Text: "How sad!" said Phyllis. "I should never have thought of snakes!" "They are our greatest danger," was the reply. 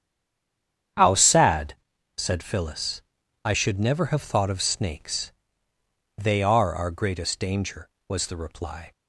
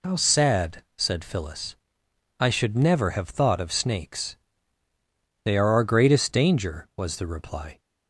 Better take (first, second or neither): second